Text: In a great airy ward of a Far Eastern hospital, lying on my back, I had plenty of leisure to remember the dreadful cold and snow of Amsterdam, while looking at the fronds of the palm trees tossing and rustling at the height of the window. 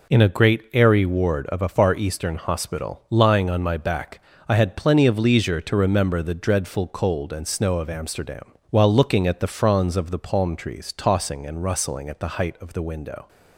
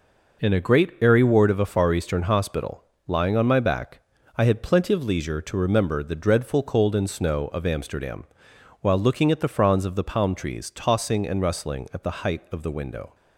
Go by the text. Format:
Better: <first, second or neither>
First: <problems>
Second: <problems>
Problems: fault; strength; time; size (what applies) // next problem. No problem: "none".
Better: neither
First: none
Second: none